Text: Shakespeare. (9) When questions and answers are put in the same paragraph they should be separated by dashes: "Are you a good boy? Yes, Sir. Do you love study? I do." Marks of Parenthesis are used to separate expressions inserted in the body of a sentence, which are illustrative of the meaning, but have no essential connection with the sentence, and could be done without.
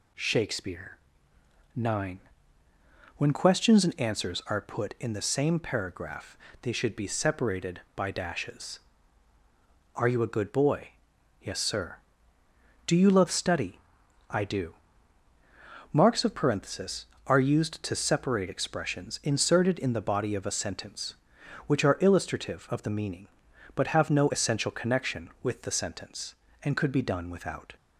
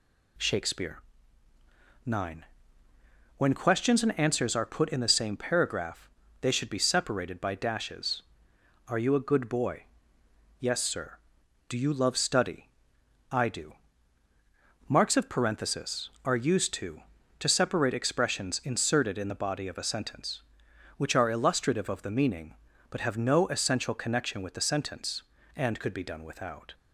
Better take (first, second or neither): first